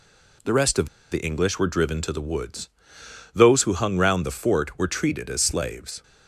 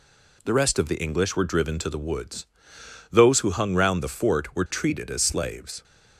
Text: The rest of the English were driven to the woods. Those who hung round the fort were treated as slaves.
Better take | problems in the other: second | pauses between "of" and "the"; slight; at 0.8 s; 0.24 s long

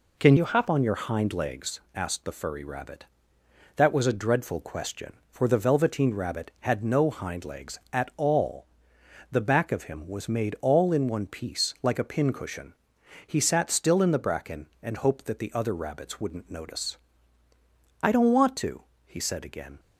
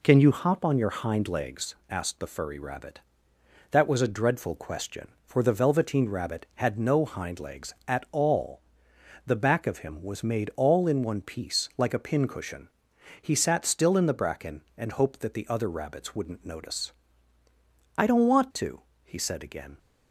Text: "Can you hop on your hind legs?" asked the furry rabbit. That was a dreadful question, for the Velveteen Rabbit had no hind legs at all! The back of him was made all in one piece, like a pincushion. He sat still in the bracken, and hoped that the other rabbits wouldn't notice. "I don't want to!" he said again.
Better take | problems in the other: second | changes voice from "you" to "hop"; from 0.3 to 0.6 s; 0.3 s long

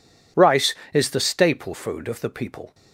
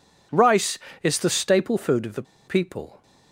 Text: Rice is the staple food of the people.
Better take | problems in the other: first | pauses between "the" and "people"; slight; at 2.2 s; 0.24 s long

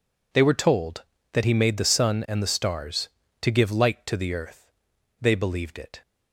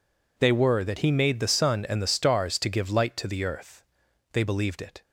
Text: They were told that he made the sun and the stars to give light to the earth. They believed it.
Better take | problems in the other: first | skips "told"; at 0.8 s

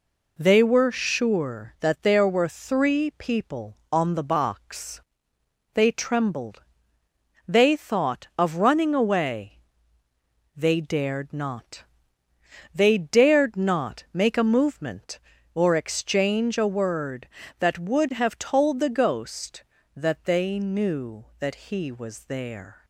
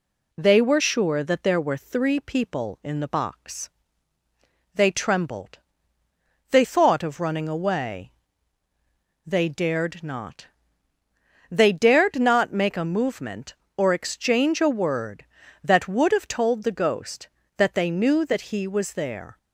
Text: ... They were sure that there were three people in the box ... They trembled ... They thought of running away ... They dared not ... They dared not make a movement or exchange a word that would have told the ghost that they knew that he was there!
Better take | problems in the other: second | says "on" for "in"; at 3.9 s

